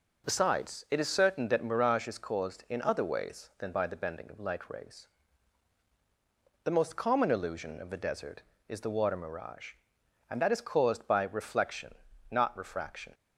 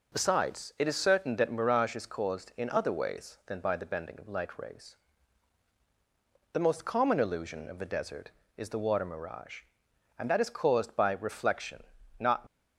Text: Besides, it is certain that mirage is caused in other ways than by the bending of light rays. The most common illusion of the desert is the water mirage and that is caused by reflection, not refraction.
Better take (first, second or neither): first